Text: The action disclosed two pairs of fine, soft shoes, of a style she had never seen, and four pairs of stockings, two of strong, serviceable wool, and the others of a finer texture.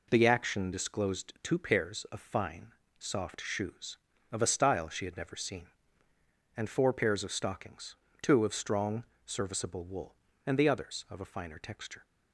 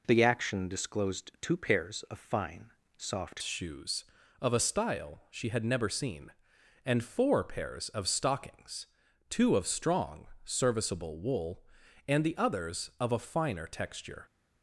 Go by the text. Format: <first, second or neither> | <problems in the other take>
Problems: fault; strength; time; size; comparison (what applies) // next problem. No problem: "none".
first | changes voice at "shoes"; from 3.4 s on; 10.8 s long